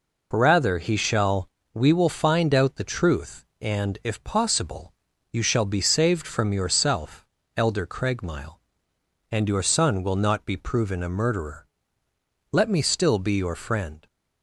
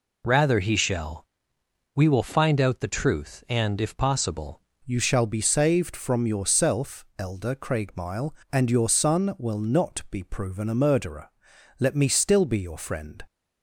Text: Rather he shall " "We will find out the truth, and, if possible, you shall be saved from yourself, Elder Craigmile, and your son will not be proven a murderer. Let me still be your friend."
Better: first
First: none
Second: changes voice at "you"; from 4.8 s on; 8.4 s long

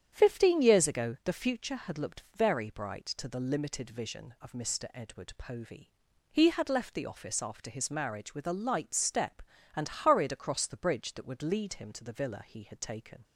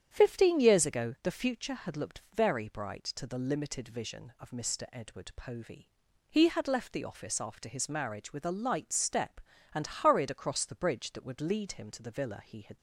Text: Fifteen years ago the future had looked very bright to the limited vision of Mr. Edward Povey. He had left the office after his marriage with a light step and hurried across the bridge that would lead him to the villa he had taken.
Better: first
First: starts louder than the rest; strong; until 1.1 s; 8.5 dB // pauses between "looked" and "very"; slight; at 2.2 s; 0.16 s long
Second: starts louder than the rest; strong; until 1.1 s; 8.5 dB // pauses between "looked" and "very"; slight; at 2.1 s; 0.16 s long // stops before "taken"; at 12.7 s

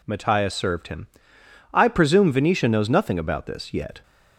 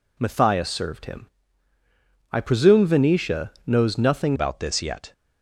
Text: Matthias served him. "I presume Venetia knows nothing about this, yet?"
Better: first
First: none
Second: changes voice at "about"; from 4.3 s on; 0.8 s long

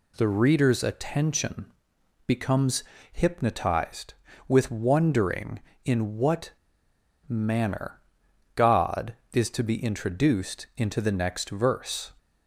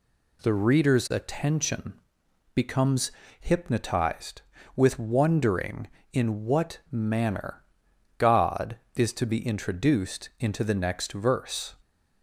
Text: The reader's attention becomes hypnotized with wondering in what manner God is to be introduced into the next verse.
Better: second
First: pauses between "attention" and "becomes"; noticeable; at 1.6 s; 0.62 s long // pauses between "becomes" and "hypnotized"; slight; at 2.8 s; 0.28 s long // pauses between "what" and "manner"; noticeable; at 6.5 s; 0.75 s long // pauses between "manner" and "God"; noticeable; at 8.0 s; 0.54 s long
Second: pauses between "attention" and "becomes"; noticeable; at 1.9 s; 0.62 s long // pauses between "becomes" and "hypnotized"; slight; at 3.1 s; 0.28 s long // pauses between "manner" and "God"; noticeable; at 7.6 s; 0.54 s long

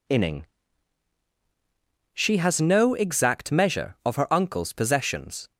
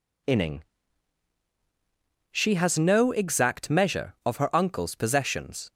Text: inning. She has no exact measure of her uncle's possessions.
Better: neither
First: none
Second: none

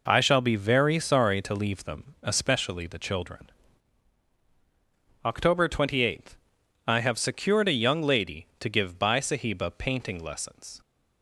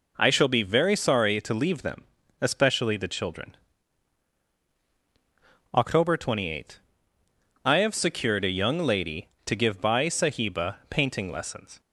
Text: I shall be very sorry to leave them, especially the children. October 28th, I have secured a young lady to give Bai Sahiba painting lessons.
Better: neither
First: none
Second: none

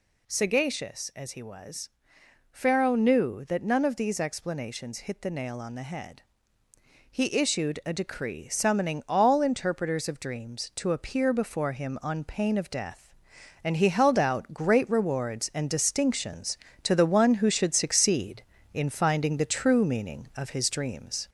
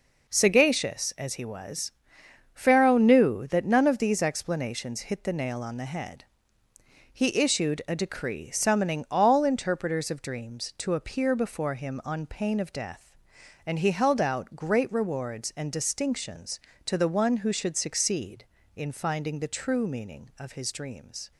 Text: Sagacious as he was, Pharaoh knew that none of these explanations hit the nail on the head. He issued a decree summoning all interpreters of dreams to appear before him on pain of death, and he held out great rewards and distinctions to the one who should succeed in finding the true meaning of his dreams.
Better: second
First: gets louder; slight; throughout; 3 dB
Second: none

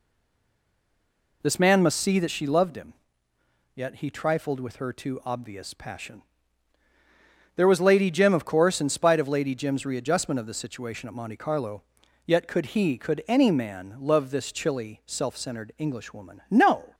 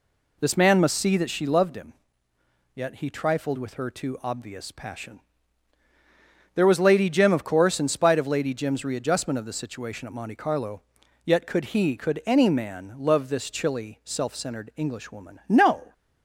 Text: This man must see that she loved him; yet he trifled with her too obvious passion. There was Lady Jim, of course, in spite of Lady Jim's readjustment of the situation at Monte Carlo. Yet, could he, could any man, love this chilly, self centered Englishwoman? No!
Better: second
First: stays silent before the first word; noticeable; until 1.4 s; 1.4 s long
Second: none

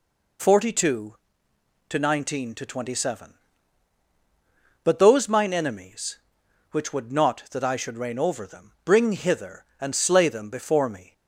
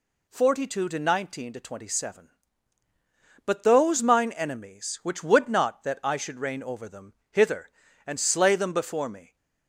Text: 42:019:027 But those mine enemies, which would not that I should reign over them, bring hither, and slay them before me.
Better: first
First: none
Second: skips "bring"; at 7.2 s

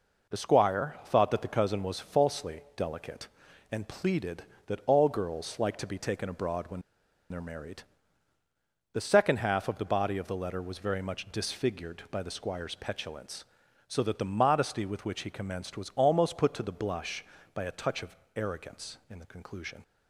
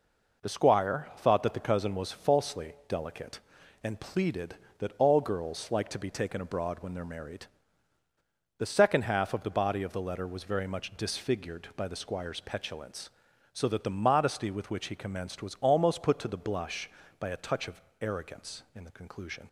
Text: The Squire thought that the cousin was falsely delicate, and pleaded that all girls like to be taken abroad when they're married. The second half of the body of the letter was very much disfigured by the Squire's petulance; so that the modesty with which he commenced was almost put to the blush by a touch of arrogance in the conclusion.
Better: second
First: pauses between "when" and "they're"; noticeable; at 6.8 s; 0.48 s long // pauses between "of" and "arrogance"; slight; at 18.1 s; 0.18 s long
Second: pauses between "of" and "arrogance"; slight; at 17.8 s; 0.18 s long

